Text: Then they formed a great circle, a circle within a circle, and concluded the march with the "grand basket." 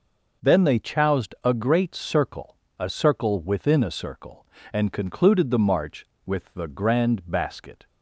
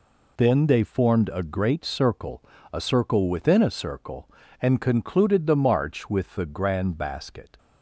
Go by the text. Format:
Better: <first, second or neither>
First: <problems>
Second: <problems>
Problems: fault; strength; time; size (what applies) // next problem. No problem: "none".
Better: second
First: says "choused" for "formed"; at 0.7 s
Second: none